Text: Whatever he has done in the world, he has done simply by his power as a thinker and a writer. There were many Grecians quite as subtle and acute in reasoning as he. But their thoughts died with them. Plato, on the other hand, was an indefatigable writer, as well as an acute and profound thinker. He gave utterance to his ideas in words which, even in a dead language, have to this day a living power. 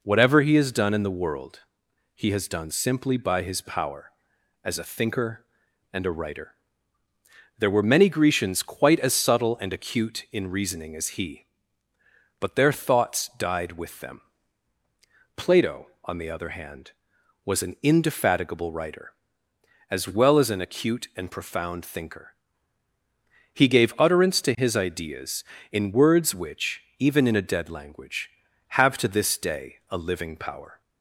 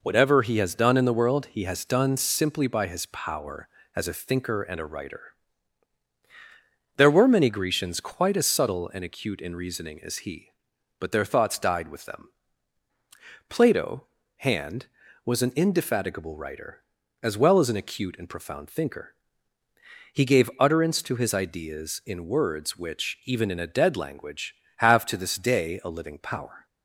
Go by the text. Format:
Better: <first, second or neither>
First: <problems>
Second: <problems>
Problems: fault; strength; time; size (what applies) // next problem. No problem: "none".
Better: first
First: none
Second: skips "on the other"; at 14.2 s